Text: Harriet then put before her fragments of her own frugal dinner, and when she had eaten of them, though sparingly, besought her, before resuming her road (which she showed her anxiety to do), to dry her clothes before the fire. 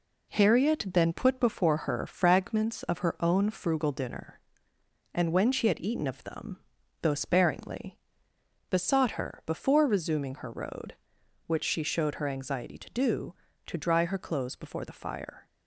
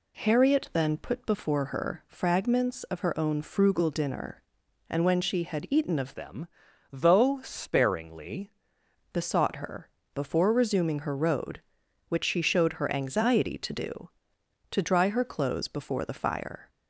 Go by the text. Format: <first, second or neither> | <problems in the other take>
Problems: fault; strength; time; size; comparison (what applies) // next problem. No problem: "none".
first | changes voice from "them" to "sparingly"; from 6.1 to 8.4 s; 2.3 s long